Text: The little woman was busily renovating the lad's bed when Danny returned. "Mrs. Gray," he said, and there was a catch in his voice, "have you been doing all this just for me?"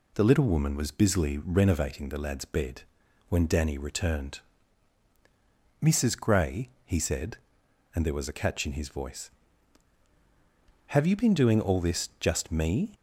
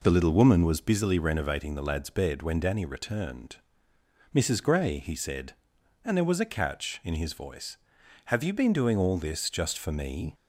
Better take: second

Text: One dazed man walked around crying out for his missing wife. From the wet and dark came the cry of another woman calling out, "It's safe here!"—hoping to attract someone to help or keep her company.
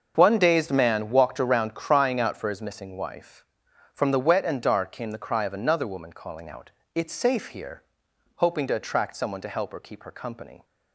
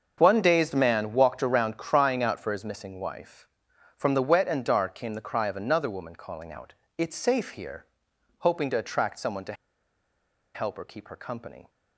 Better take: first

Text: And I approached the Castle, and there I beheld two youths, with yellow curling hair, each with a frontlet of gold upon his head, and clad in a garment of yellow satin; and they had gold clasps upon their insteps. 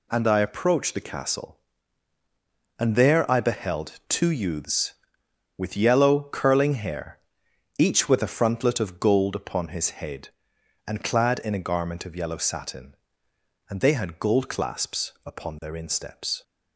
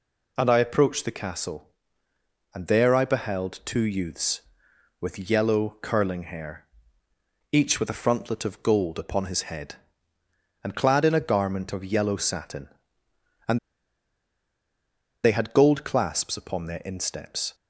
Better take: first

